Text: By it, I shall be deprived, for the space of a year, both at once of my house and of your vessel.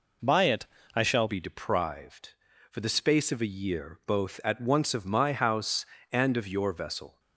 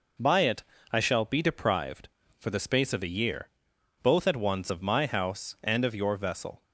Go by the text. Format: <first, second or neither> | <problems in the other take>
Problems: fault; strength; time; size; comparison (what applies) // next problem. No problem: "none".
second | changes voice at "be"; from 1.2 s on; 5.9 s long